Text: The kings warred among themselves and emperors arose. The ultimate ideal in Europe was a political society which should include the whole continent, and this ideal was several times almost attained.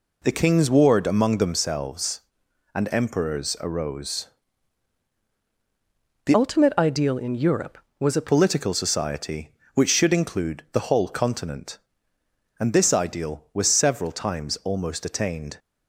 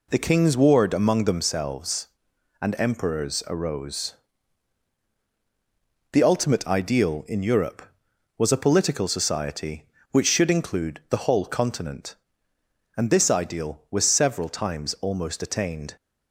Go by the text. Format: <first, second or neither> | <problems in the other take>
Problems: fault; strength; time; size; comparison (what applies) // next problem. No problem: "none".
second | changes voice from "ultimate" to "a"; from 6.3 to 8.2 s; 1.9 s long